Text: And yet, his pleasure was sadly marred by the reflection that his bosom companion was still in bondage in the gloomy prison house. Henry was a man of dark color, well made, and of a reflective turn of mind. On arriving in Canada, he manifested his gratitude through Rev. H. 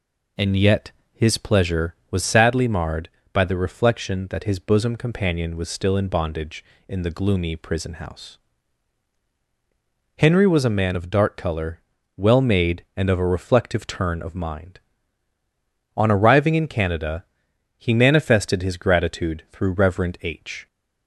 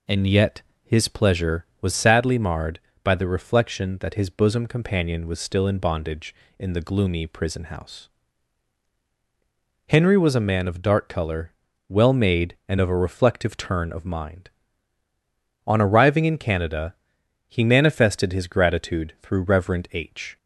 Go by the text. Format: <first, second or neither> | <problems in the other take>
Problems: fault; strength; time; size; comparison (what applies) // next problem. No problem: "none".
neither | none